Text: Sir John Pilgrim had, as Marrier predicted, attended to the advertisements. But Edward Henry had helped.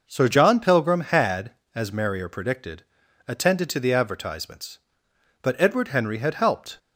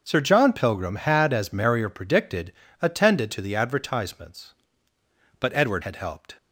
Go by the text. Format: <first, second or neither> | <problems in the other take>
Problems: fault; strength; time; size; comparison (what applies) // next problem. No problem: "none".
first | starts louder than the rest; noticeable; until 1.0 s; 6 dB // skips "Henry"; at 5.8 s